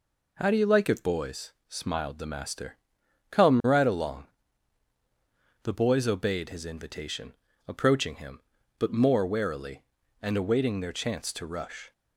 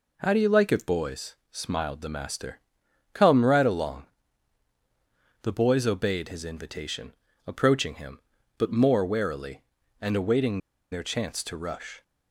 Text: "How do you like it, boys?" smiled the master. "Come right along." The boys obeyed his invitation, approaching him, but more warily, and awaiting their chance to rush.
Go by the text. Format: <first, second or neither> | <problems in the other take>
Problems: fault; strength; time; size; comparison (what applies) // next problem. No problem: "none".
first | pauses between "awaiting" and "their"; slight; at 10.5 s; 0.34 s long